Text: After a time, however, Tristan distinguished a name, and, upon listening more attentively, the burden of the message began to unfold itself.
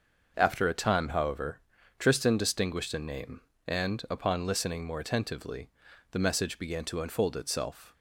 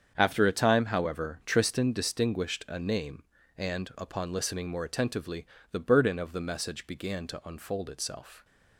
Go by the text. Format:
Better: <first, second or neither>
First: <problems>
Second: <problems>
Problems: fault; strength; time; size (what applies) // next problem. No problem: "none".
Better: second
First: starts louder than the rest; until 1.3 s; 6 dB // skips "burden of the"; at 6.1 s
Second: starts louder than the rest; strong; until 1.1 s; 7.5 dB